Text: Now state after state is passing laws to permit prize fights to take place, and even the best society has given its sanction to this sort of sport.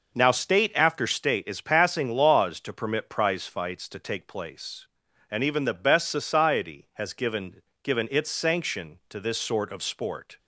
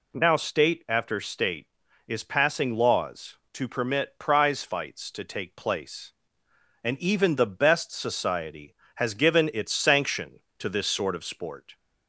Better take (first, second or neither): second